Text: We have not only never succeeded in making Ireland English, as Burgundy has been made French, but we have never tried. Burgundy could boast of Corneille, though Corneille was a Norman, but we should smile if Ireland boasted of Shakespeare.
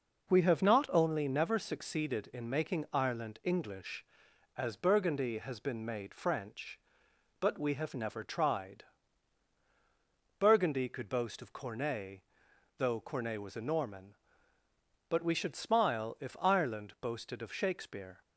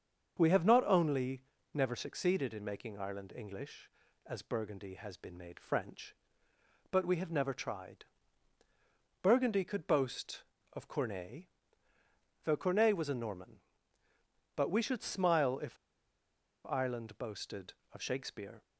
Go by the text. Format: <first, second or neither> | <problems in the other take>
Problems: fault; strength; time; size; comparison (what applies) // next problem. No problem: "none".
first | starts louder than the rest; until 1.4 s; 7 dB // pauses between "only" and "never"; slight; at 1.4 s; 0.32 s long // pauses between "if" and "Ireland"; noticeable; at 15.7 s; 0.92 s long